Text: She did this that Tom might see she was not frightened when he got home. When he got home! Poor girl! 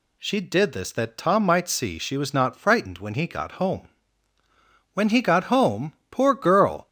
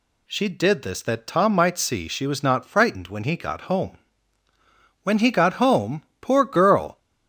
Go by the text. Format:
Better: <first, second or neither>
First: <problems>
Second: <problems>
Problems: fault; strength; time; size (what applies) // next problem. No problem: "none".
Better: neither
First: none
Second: none